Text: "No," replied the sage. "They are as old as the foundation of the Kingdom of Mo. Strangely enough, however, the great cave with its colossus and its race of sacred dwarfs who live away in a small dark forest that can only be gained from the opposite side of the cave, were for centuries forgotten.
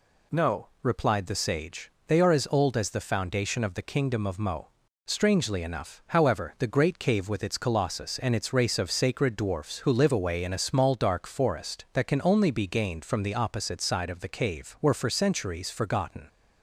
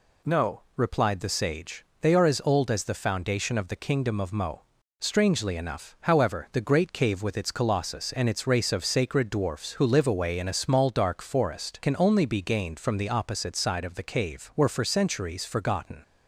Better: first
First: none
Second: skips "that"; at 11.8 s

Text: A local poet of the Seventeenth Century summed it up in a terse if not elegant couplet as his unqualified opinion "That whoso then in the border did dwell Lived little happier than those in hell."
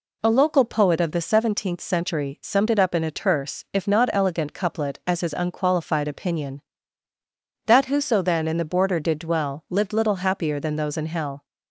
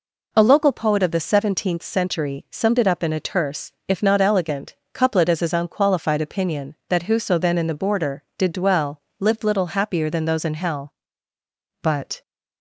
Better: first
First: none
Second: pauses between "elegant" and "couplet"; slight; at 4.7 s; 0.18 s long // pauses between "dwell" and "Lived"; slight; at 9.0 s; 0.18 s long // goes on to say "But"; slight; from 11.8 s on; 0.40 s long

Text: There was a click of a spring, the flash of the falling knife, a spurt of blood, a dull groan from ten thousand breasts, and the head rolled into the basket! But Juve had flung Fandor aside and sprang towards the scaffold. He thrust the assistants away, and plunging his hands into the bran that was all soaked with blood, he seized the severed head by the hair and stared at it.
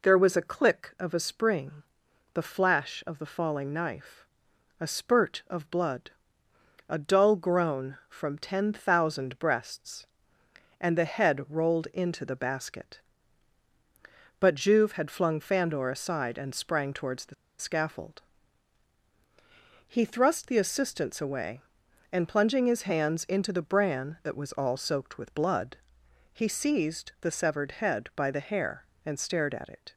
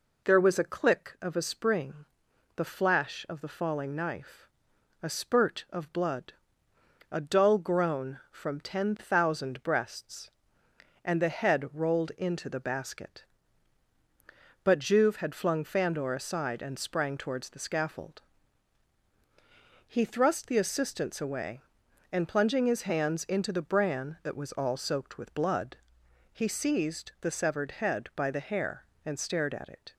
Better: second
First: pauses between "the" and "scaffold"; slight; at 17.3 s; 0.24 s long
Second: none

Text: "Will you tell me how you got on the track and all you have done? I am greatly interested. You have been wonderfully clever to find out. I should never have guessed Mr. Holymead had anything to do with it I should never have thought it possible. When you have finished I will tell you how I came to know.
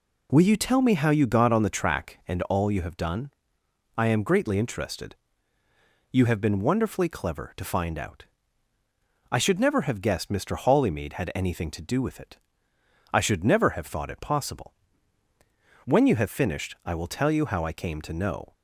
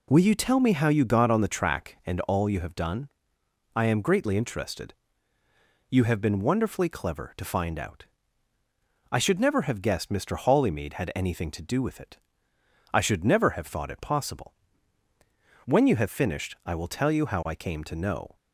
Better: neither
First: pauses between "it" and "I"; noticeable; at 12.3 s; 0.74 s long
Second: pauses between "it" and "I"; noticeable; at 12.1 s; 0.74 s long

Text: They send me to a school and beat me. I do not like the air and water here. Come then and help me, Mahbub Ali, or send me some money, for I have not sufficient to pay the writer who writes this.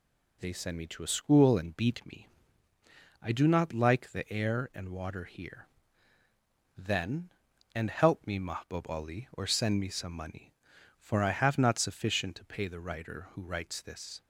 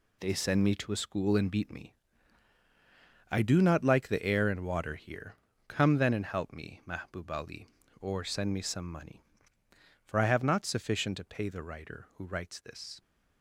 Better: second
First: skips "Come"; at 6.2 s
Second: none

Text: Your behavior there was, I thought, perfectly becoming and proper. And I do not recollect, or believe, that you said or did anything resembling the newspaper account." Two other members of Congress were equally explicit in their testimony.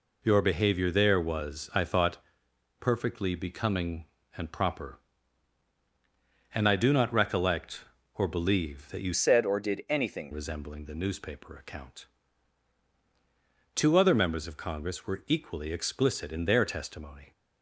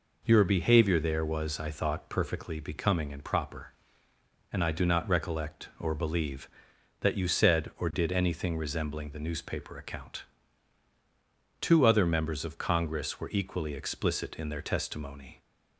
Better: second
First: changes voice from "said" to "anything"; from 9.1 to 10.3 s; 1.2 s long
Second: none

